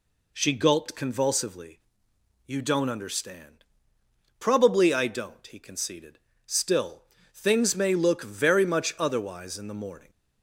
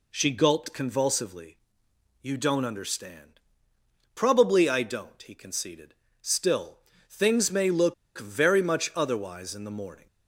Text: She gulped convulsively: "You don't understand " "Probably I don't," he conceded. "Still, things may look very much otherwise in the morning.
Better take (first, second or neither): first